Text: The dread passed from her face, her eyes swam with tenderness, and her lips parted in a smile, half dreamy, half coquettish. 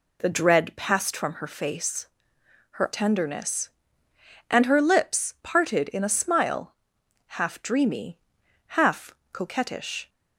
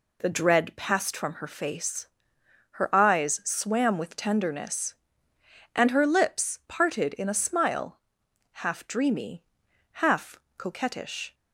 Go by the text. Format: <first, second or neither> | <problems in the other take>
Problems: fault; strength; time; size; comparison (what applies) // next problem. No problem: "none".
second | skips "eyes swam with"; at 2.9 s // pauses between "half" and "coquettish"; slight; at 9.1 s; 0.20 s long; slight in the second